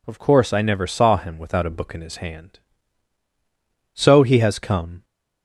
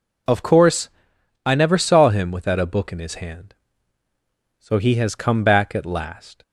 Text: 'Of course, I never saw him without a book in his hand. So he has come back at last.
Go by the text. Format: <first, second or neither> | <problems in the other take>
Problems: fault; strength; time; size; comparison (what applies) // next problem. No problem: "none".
second | stops before "back at last"; at 5.0 s